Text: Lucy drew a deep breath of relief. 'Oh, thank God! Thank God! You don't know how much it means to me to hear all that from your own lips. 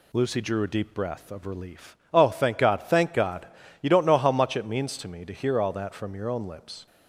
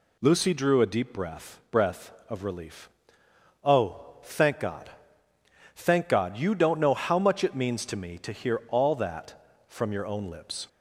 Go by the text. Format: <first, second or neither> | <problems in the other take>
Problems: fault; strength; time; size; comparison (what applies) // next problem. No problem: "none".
first | says "breath" twice; at 1.6 s